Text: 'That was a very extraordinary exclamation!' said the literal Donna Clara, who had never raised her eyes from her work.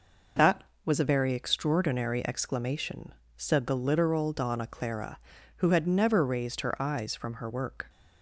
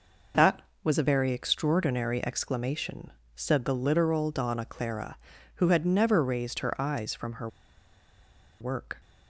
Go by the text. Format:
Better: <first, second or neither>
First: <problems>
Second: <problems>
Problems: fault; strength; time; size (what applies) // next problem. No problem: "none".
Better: first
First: none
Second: pauses between "her" and "work"; at 7.4 s; 1.1 s long